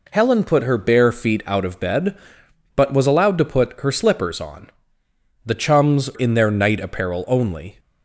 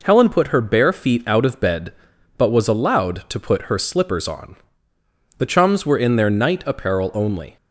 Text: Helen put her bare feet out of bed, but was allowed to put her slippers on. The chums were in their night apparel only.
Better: second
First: skips "were"; at 6.1 s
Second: none

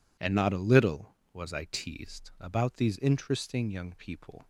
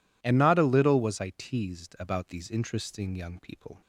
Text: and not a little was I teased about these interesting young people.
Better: neither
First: none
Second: none

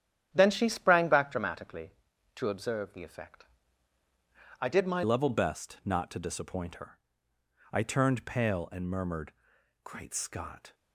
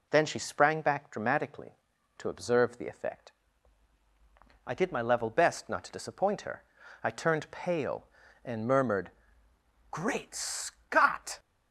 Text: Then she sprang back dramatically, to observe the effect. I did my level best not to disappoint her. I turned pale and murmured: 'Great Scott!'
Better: second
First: starts louder than the rest; strong; until 1.3 s; 10 dB // changes voice at "level"; from 5.0 s on; 5.7 s long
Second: none

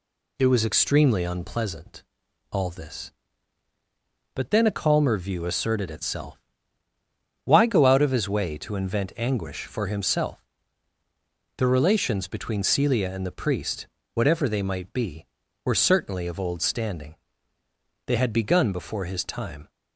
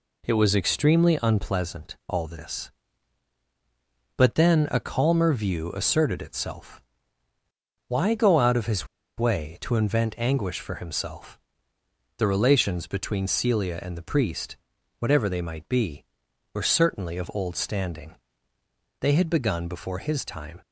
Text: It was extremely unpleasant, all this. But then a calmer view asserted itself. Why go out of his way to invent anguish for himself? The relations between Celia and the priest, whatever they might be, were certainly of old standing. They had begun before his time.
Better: first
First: none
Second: pauses between "his" and "way"; slight; at 8.8 s; 0.31 s long

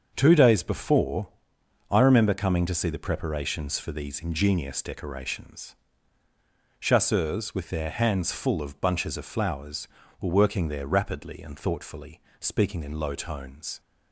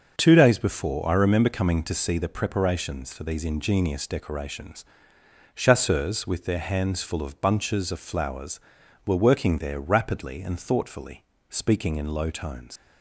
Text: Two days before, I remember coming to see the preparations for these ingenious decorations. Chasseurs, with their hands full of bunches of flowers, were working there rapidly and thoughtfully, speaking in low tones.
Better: first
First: starts louder than the rest; until 1.1 s; 6.5 dB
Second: starts louder than the rest; until 1.1 s; 6 dB // leaves "tones" unfinished; at 12.7 s; 85 ms

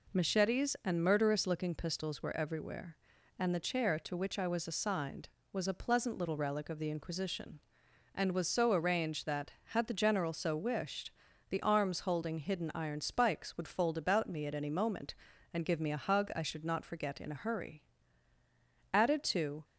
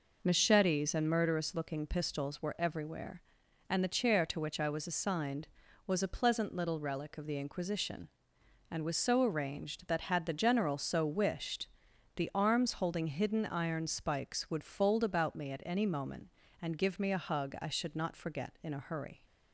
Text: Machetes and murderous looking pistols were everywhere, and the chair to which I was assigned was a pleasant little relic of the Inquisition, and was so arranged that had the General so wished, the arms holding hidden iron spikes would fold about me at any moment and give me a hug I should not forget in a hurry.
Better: second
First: goes on to say "Added to"; noticeable; from 18.9 s on; 0.70 s long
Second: none

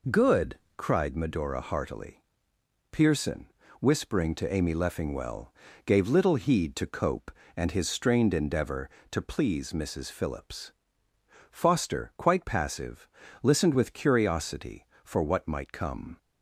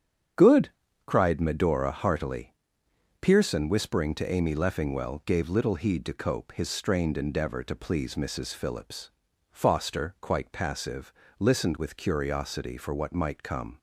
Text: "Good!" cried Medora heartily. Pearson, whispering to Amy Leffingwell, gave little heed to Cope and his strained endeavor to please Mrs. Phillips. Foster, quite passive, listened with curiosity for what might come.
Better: first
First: none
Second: starts louder than the rest; strong; until 1.7 s; 8 dB // skips "and"; at 6.5 s

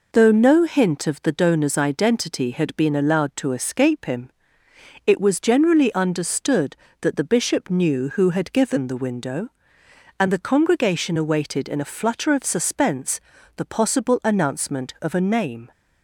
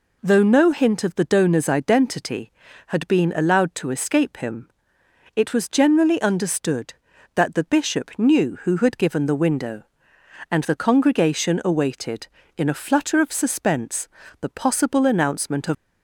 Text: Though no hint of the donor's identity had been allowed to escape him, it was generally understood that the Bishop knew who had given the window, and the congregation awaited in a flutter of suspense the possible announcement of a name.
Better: first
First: pauses between "suspense" and "the"; at 13.1 s; 0.38 s long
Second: pauses between "suspense" and "the"; slight; at 14.0 s; 0.32 s long // stops before "a name"; at 15.7 s

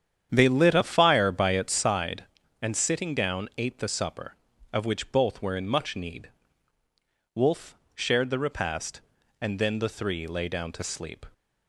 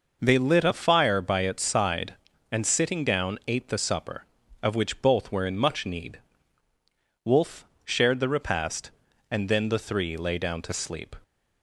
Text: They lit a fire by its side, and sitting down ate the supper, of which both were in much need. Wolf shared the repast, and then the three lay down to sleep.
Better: second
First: starts louder than the rest; strong; until 1.9 s; 9 dB // pauses between "Wolf" and "shared"; slight; at 7.7 s; 0.20 s long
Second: pauses between "Wolf" and "shared"; slight; at 7.6 s; 0.20 s long

